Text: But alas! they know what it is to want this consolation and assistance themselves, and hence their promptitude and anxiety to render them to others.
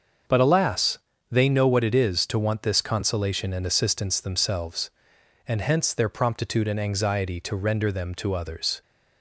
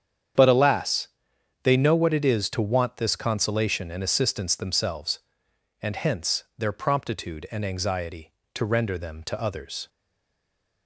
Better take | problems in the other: first | starts louder than the rest; strong; until 1.9 s; 8.5 dB; also in the first // stays silent after the last word; from 9.8 s on; 1.0 s long

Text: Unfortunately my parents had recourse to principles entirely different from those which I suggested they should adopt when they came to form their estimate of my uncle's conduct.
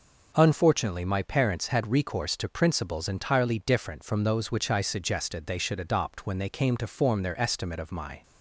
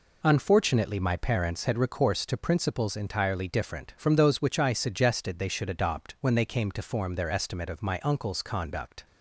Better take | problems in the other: second | stops before "uncle's conduct"; at 8.2 s

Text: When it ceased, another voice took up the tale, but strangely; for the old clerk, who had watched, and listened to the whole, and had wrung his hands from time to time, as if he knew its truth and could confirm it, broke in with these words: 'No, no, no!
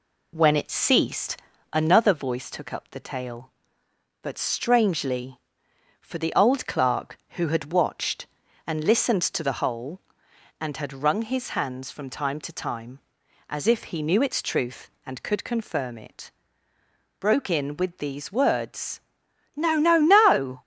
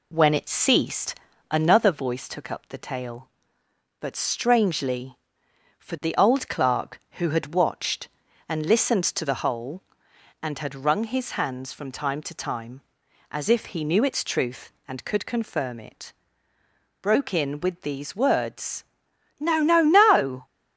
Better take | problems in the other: neither | none

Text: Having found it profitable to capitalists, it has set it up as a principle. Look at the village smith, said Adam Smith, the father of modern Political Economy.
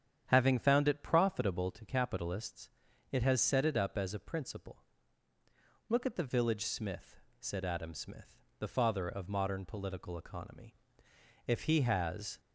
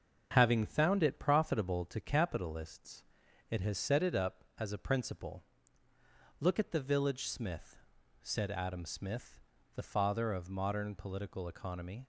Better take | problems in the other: second | starts louder than the rest; strong; until 1.2 s; 9 dB; also in the second // goes on to say "If he has"; noticeable; from 11.4 s on; 0.94 s long

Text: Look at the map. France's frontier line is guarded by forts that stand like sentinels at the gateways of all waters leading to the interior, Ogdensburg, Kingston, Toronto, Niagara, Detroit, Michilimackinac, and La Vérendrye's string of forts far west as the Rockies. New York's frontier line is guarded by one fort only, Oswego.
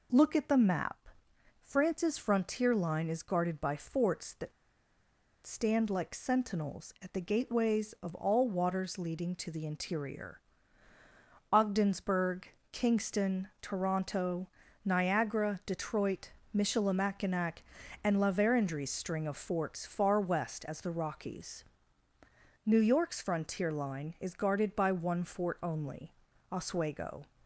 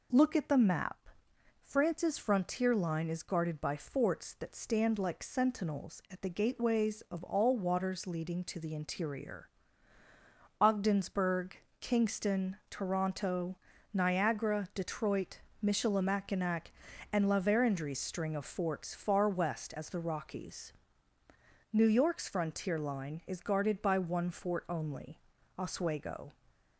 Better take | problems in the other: second | pauses between "that" and "stand"; noticeable; at 4.5 s; 0.92 s long

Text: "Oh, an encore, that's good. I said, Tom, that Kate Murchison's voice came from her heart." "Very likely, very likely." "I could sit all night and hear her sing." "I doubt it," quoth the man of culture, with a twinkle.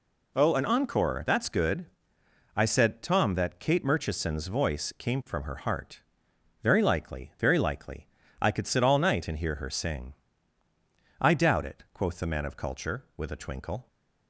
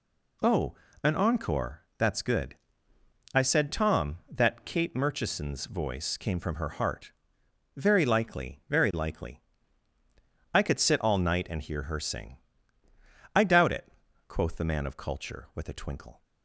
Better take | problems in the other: neither | none

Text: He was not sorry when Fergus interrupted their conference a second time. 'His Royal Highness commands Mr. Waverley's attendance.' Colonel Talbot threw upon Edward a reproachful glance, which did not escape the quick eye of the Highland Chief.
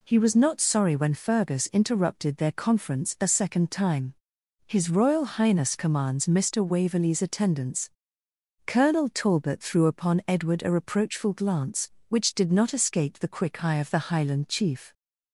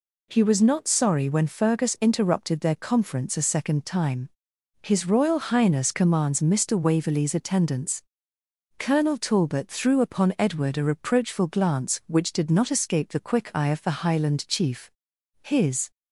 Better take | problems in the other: first | goes on to say "His"; from 15.4 s on; 0.50 s long

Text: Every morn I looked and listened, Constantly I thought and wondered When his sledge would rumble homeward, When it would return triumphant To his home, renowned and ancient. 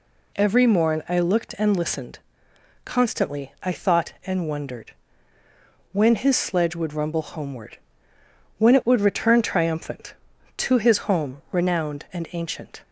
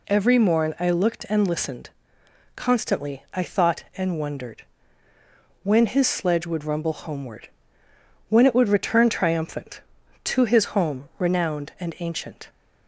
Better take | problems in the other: neither | pauses between "wondered" and "When"; noticeable; the same in both

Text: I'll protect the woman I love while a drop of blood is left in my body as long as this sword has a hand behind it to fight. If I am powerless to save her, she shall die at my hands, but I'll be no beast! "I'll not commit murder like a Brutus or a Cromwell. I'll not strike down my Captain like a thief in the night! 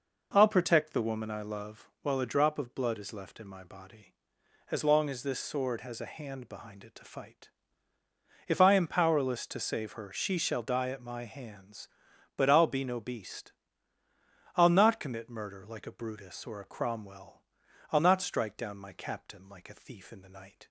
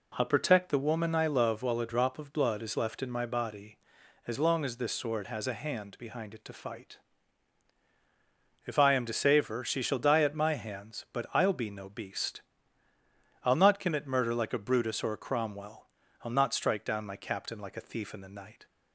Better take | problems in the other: first | skips "powerless"; at 9.0 s

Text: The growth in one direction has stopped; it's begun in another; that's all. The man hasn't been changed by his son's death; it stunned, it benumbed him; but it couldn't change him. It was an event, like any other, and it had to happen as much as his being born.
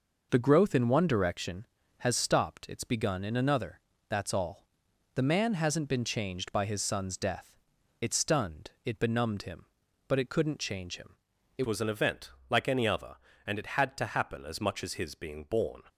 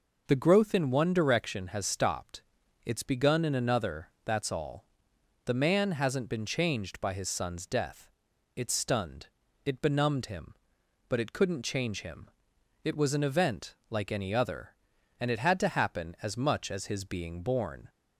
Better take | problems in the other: second | changes voice at "was"; from 11.6 s on; 4.2 s long

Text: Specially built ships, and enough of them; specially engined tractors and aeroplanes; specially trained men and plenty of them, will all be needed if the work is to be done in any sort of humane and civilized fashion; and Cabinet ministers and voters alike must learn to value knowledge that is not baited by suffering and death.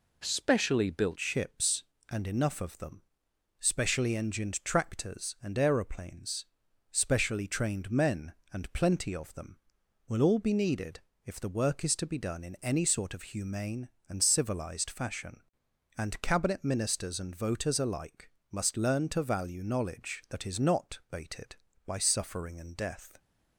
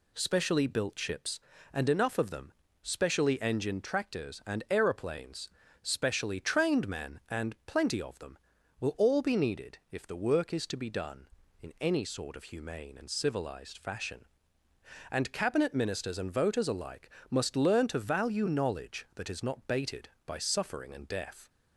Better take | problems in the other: second | changes voice at "ships"; from 1.1 s on; 22.0 s long // pauses between "needed" and "if"; slight; at 11.0 s; 0.24 s long // pauses between "alike" and "must"; slight; at 18.3 s; 0.20 s long; slight in the second

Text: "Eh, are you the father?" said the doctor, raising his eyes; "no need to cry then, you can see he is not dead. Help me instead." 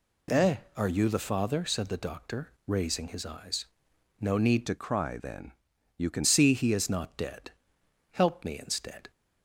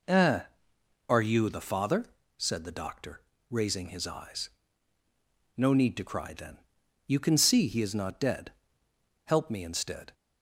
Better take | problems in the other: second | changes voice from "to" to "can"; from 4.6 to 6.2 s; 1.6 s long

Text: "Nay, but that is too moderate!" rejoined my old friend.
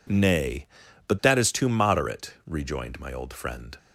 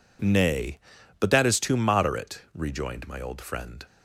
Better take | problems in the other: neither | none

